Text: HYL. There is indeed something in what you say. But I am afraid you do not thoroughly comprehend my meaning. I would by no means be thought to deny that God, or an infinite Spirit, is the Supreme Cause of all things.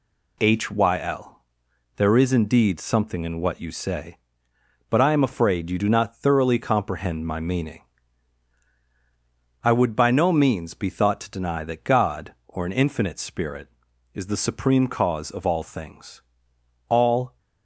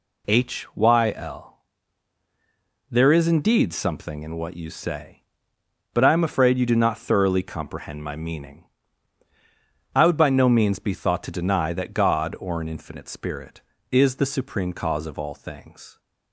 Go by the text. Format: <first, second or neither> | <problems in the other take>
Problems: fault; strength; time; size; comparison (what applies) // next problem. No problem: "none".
second | goes on to say "All"; from 16.8 s on; 0.50 s long